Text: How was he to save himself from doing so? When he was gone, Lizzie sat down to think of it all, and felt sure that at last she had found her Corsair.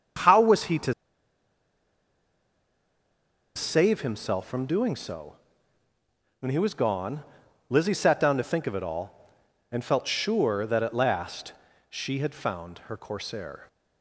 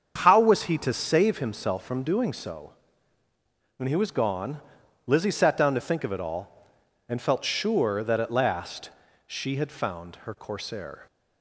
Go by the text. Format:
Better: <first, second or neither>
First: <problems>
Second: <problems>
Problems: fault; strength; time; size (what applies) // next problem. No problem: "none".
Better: second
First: starts louder than the rest; strong; until 3.8 s; 7.5 dB // pauses between "to" and "save"; strong; at 0.9 s; 2.6 s long // pauses between "last" and "she"; at 11.5 s; 0.38 s long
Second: starts louder than the rest; strong; until 1.1 s; 7 dB // pauses between "last" and "she"; at 8.8 s; 0.38 s long